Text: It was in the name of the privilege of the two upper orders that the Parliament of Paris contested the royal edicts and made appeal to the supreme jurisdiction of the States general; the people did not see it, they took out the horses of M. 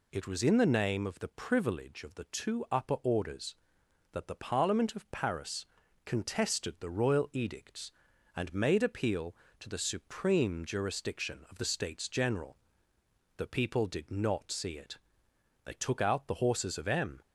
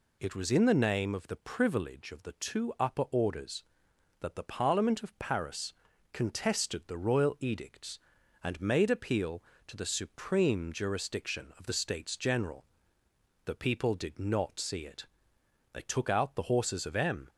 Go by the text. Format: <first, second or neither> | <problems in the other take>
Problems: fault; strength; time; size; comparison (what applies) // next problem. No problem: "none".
neither | pauses between "Paris" and "contested"; the same in both